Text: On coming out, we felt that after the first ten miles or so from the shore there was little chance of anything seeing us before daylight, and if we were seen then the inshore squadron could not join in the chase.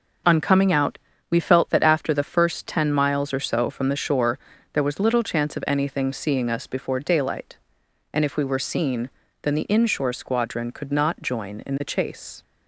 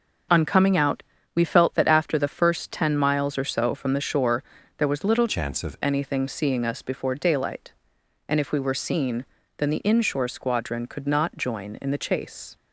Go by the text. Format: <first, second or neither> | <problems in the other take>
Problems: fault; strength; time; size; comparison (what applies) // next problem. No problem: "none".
first | starts louder than the rest; until 1.6 s; 6.5 dB; also in the first // pauses between "shore" and "there"; slight; at 4.4 s; 0.34 s long; slight in the first // changes voice from "chance" to "of"; from 5.2 to 5.7 s; 0.5 s long // pauses between "seen" and "then"; slight; at 9.2 s; 0.32 s long; slight in the first